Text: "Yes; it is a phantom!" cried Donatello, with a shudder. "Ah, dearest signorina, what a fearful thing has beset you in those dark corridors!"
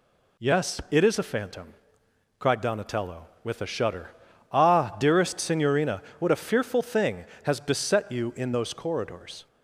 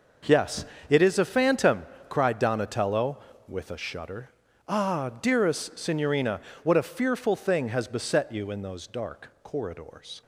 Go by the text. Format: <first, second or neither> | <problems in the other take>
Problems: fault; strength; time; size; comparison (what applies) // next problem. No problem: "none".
second | skips "dark"; at 8.7 s